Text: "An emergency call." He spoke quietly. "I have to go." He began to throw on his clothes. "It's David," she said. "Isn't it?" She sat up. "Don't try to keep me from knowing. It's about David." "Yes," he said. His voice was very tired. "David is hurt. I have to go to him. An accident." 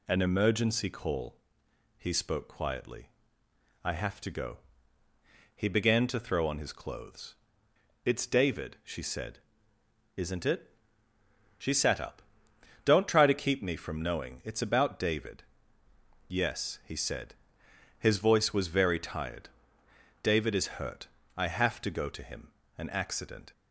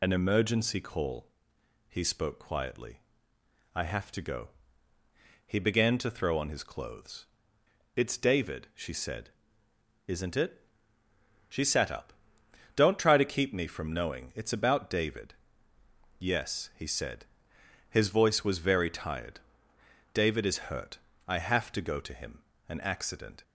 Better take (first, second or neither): first